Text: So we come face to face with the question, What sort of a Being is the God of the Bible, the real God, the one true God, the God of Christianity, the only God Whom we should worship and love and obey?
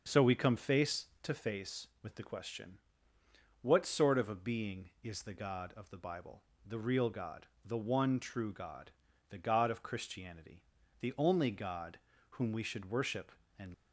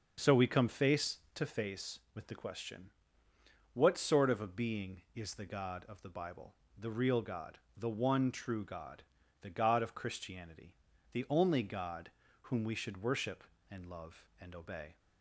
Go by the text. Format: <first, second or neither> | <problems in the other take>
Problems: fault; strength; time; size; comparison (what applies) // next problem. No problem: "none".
second | starts louder than the rest; until 1.0 s; 6.5 dB; also in the second // pauses between "God" and "Whom"; slight; at 11.9 s; 0.32 s long; slight in the second // stops before "love and obey"; at 13.7 s